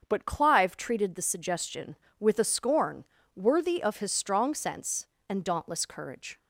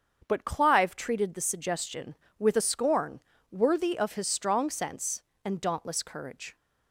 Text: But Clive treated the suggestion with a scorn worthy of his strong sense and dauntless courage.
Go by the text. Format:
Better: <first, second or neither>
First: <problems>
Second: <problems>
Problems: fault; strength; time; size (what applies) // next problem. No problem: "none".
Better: neither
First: starts louder than the rest; until 1.0 s; 6.5 dB // pauses between "scorn" and "worthy"; slight; at 3.0 s; 0.32 s long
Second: starts louder than the rest; until 1.2 s; 7 dB // pauses between "scorn" and "worthy"; slight; at 3.1 s; 0.32 s long